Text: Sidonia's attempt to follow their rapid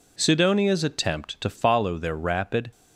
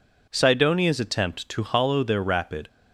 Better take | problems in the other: first | says "hollow" for "follow"; at 1.6 s

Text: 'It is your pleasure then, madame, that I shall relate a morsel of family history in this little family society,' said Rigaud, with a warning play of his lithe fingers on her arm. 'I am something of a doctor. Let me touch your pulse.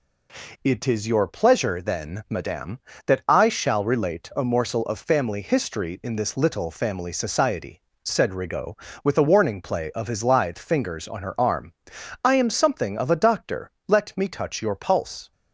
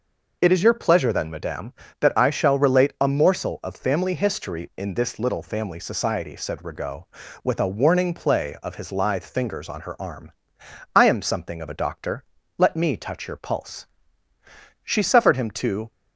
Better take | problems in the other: first | goes on to say "She suffered him to"; noticeable; from 14.8 s on; 1.0 s long

